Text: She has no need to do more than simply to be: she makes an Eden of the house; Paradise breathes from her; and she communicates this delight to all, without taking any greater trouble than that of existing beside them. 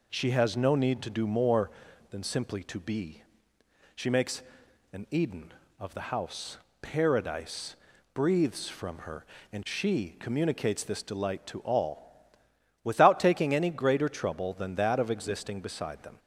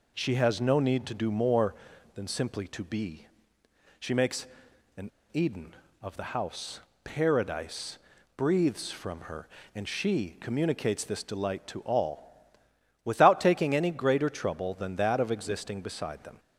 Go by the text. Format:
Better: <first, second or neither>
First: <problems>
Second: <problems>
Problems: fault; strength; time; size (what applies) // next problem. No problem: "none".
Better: first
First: pauses between "makes" and "an"; noticeable; at 4.4 s; 0.48 s long // pauses between "Paradise" and "breathes"; slight; at 7.7 s; 0.36 s long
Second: pauses between "makes" and "an"; noticeable; at 4.4 s; 0.48 s long // pauses between "an" and "Eden"; slight; at 5.1 s; 0.20 s long // pauses between "Paradise" and "breathes"; slight; at 7.9 s; 0.36 s long